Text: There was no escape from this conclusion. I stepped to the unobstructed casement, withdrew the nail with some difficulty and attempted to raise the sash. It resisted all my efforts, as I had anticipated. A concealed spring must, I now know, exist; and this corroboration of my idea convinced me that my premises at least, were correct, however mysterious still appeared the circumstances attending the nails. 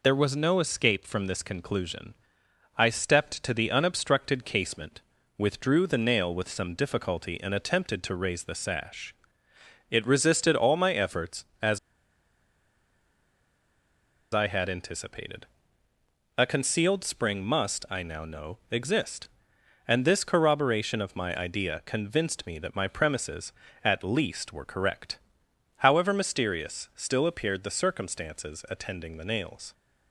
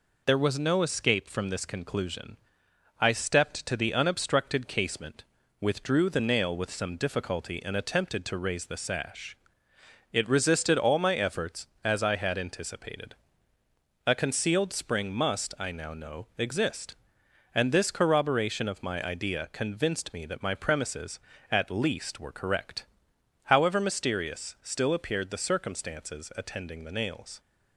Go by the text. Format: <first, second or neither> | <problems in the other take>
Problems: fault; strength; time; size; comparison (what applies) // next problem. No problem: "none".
second | pauses between "as" and "I"; strong; at 11.7 s; 2.5 s long